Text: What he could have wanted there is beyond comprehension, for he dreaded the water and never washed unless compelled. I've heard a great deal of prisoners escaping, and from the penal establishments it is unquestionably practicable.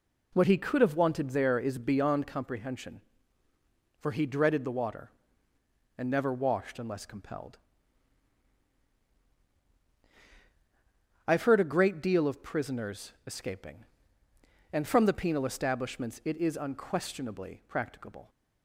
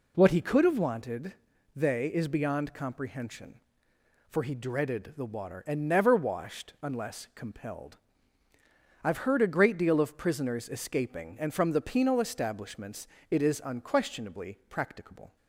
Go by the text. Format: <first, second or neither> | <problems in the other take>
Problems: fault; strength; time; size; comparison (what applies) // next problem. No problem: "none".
first | says "they" for "there"; at 1.7 s // pauses between "establishments" and "it"; slight; at 13.0 s; 0.22 s long